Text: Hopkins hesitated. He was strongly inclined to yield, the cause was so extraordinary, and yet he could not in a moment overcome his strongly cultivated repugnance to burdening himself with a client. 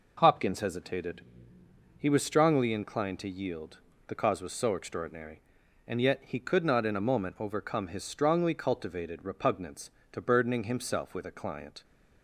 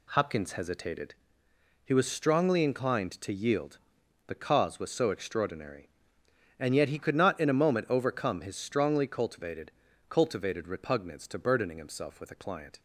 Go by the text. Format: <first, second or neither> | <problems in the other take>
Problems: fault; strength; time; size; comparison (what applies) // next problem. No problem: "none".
first | says "cultivated" twice; at 10.0 s